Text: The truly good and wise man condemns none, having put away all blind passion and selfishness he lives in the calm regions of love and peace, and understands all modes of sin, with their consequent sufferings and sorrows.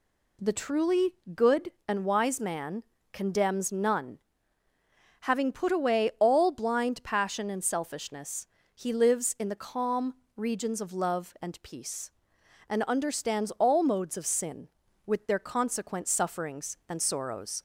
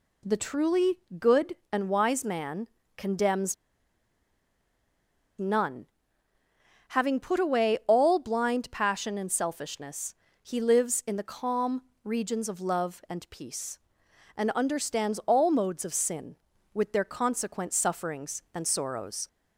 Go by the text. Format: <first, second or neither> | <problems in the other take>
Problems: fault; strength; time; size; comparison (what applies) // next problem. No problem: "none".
first | pauses between "truly" and "good"; slight; at 0.9 s; 0.18 s long; slight in the first // pauses between "man" and "condemns"; slight; at 2.6 s; 0.28 s long; slight in the first // pauses between "condemns" and "none"; strong; at 3.5 s; 1.8 s long // pauses between "selfishness" and "he"; slight; at 10.1 s; 0.28 s long; slight in the first // pauses between "calm" and "regions"; slight; at 11.8 s; 0.24 s long; slight in the first